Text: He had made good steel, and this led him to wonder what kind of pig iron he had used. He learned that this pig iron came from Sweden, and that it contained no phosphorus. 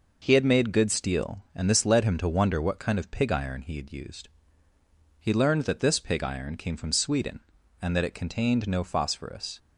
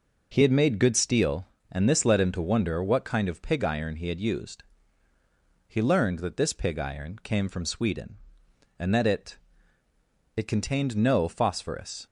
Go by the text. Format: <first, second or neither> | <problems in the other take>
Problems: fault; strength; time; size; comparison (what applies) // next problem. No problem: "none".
first | says "it" twice; at 10.3 s